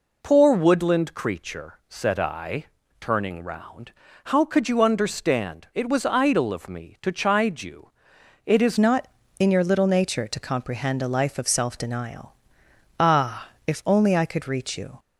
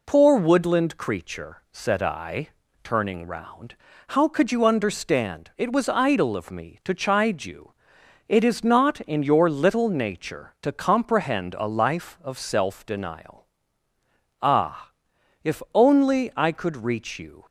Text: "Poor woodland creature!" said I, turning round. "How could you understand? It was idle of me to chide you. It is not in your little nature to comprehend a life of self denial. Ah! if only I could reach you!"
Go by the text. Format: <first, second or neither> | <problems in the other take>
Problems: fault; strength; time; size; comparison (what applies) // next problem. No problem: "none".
second | changes voice at "not"; from 8.7 s on; 6.2 s long